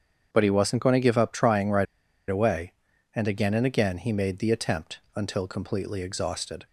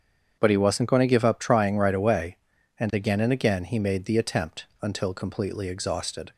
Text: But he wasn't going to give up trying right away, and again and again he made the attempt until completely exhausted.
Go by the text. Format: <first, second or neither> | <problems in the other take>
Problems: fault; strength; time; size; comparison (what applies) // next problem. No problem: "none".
second | starts louder than the rest; strong; until 1.3 s; 7.5 dB; strong in the second // pauses between "right" and "away"; at 1.8 s; 0.44 s long